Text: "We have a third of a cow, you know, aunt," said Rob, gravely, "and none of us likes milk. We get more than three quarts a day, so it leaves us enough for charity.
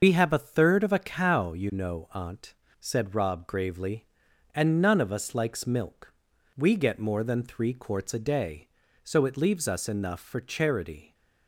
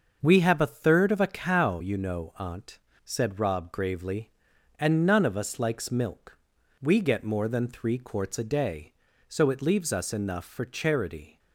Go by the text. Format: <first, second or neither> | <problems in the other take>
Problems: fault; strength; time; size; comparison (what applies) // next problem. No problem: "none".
second | loses the start of "We"; at 0.0 s; 80 ms // starts louder than the rest; until 1.0 s; 6 dB; also in the second